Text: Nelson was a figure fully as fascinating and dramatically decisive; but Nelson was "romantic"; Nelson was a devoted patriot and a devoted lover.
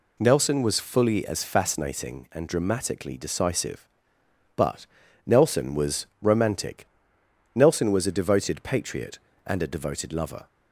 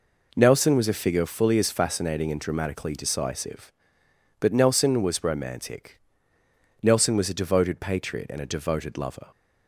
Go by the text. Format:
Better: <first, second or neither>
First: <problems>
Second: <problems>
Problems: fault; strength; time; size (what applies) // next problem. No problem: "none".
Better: second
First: skips "a figure"; at 0.8 s // pauses between "but" and "Nelson"; at 4.8 s; 0.40 s long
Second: none